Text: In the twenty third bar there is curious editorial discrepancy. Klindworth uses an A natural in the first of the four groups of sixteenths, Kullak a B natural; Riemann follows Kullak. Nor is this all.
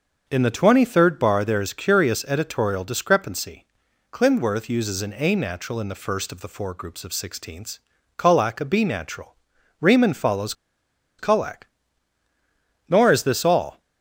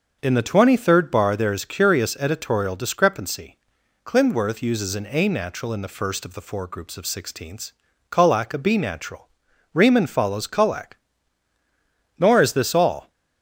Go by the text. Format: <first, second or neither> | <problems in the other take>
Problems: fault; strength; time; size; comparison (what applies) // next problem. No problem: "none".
second | starts louder than the rest; until 1.2 s; 6.5 dB; also in the second // pauses between "follows" and "Kullak"; noticeable; at 10.5 s; 0.65 s long